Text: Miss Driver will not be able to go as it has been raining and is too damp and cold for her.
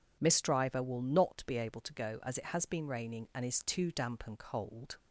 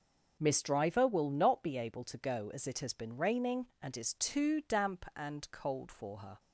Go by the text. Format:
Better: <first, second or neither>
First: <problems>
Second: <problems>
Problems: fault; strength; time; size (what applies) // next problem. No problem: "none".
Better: second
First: stops before "for her"; at 4.9 s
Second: none